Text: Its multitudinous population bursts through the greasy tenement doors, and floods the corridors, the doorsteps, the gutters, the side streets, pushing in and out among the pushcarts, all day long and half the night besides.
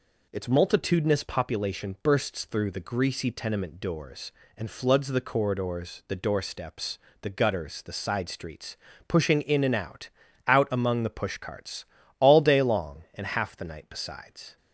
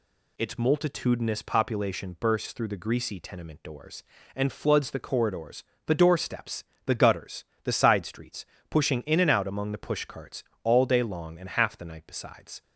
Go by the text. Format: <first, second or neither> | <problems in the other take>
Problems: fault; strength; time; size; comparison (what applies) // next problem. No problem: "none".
second | says "out" twice; at 10.4 s